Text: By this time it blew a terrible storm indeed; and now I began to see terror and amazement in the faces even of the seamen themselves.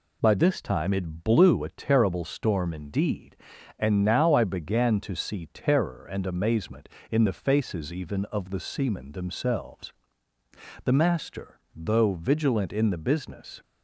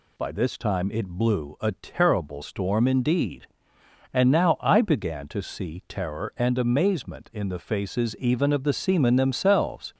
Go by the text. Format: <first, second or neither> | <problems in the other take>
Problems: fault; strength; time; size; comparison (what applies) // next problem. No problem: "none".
second | goes on to say "The master though vigilant in the business"; strong; from 10.8 s on; 2.7 s long